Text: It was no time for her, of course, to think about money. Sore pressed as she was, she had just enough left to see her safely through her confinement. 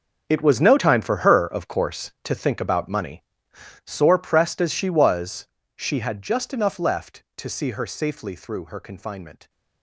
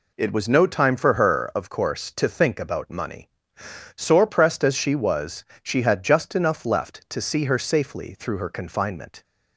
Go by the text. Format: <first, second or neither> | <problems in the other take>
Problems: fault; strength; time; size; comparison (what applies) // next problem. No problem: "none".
second | gets quieter; strong; throughout; 14 dB